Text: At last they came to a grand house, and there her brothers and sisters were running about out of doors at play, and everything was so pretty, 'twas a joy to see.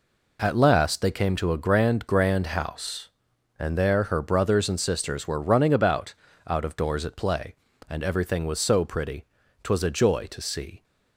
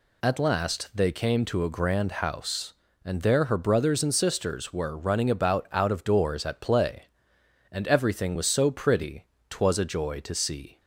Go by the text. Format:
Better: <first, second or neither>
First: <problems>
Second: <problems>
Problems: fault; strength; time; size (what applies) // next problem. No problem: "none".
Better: second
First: says "grand" twice; at 2.0 s // pauses between "about" and "out"; slight; at 6.1 s; 0.32 s long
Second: none